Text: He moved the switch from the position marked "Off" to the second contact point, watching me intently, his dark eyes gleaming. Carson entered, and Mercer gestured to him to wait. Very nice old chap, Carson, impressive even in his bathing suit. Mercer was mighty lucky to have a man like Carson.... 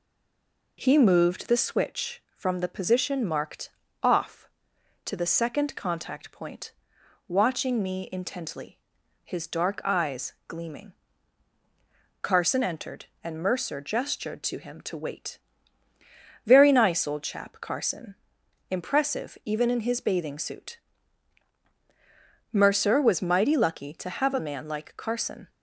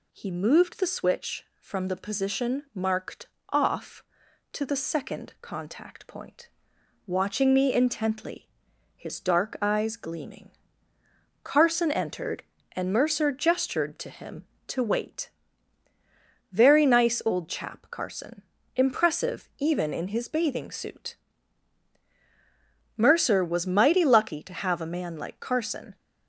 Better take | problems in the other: second | stays silent before the first word; slight; until 0.7 s; 0.7 s long // pauses between "marked" and "Off"; slight; at 3.6 s; 0.32 s long; slight in the second // pauses between "eyes" and "gleaming"; slight; at 10.3 s; 0.16 s long

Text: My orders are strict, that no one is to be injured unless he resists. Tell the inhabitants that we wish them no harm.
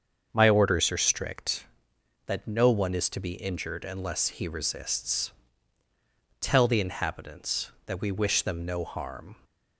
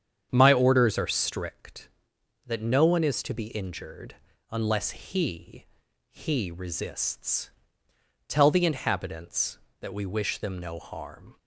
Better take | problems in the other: first | starts louder than the rest; strong; until 1.3 s; 8 dB; also in the first // pauses between "injured" and "unless"; slight; at 4.1 s; 0.36 s long // says "he" twice; at 6.0 s

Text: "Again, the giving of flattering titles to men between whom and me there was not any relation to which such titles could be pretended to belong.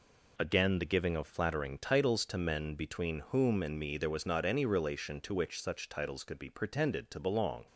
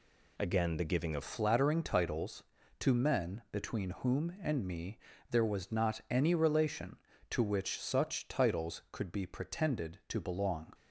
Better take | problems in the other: first | changes voice at "flattering"; from 1.2 s on; 9.5 s long // pauses between "me" and "there"; slight; at 4.9 s; 0.32 s long

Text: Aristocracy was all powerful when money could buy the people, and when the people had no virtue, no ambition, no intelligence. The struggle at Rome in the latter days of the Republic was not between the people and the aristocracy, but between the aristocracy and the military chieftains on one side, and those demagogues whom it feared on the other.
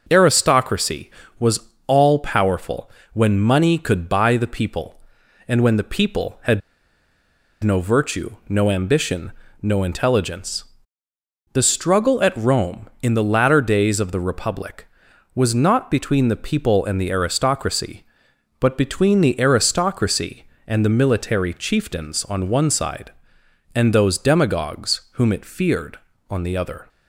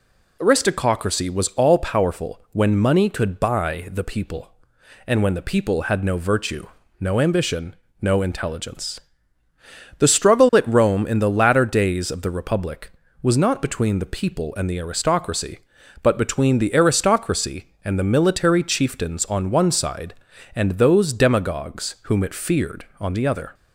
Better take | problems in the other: second | pauses between "was" and "all"; slight; at 1.6 s; 0.18 s long // pauses between "powerful" and "when"; slight; at 2.8 s; 0.22 s long // pauses between "had" and "no"; at 6.6 s; 1.0 s long

